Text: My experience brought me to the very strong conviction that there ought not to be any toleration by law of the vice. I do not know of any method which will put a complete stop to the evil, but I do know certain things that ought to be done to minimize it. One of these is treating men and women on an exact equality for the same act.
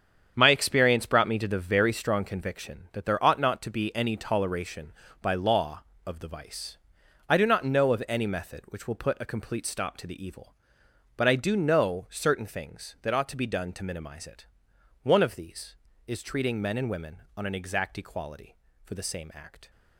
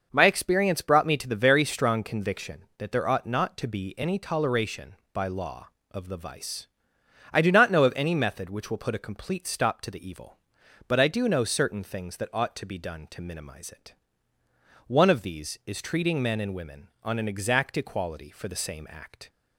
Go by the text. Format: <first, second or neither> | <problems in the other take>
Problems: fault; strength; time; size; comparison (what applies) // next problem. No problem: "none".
second | gets quieter; strong; throughout; 10 dB